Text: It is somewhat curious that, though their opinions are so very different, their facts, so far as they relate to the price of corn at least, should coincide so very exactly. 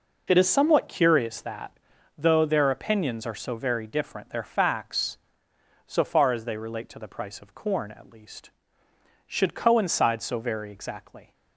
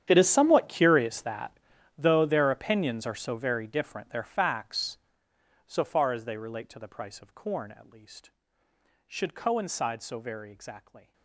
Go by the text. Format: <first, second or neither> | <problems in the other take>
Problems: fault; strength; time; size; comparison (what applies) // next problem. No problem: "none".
first | gets quieter; strong; throughout; 19 dB